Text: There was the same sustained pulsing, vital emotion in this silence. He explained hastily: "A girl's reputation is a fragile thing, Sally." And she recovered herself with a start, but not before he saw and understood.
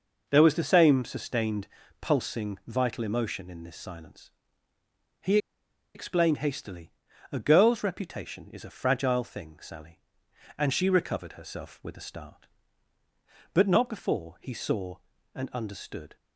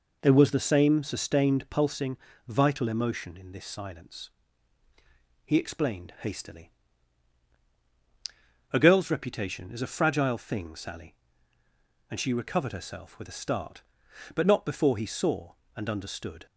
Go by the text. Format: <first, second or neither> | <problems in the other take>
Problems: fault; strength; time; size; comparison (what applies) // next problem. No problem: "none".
second | pauses between "sustained" and "pulsing"; slight; at 1.6 s; 0.34 s long // pauses between "He" and "explained"; noticeable; at 5.3 s; 0.57 s long